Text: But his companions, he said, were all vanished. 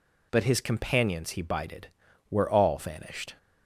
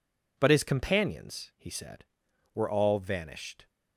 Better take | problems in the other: second | says "bided" for "said"; at 1.4 s

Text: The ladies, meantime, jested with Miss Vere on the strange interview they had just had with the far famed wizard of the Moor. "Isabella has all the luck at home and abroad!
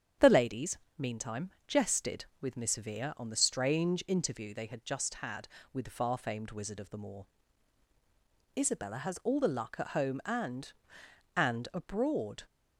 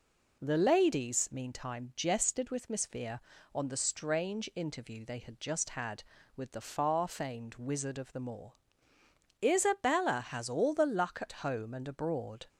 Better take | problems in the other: second | starts louder than the rest; strong; until 1.4 s; 8.5 dB // says "and" twice; at 11.3 s

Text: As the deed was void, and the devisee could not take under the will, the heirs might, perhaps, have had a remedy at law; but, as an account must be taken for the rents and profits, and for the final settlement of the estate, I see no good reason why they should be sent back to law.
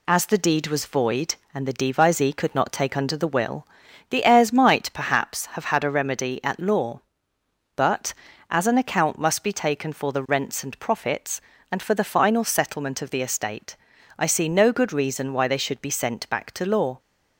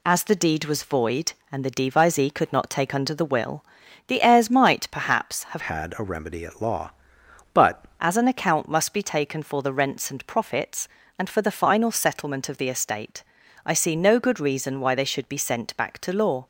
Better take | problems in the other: first | changes voice from "had" to "but"; from 5.5 to 7.8 s; 2.3 s long

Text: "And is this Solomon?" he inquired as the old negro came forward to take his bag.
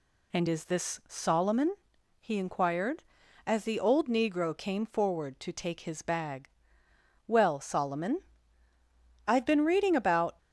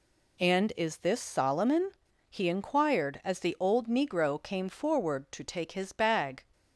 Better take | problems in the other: second | goes on to say "Well Solomon I've been reading about"; strong; from 7.2 s on; 3.1 s long

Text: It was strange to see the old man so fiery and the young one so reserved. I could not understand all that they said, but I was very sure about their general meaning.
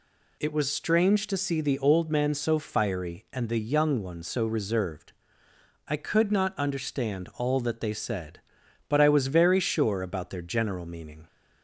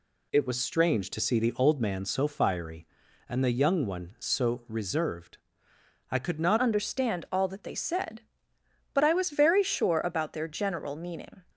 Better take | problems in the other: first | changes voice at "understand"; from 6.5 s on; 4.9 s long

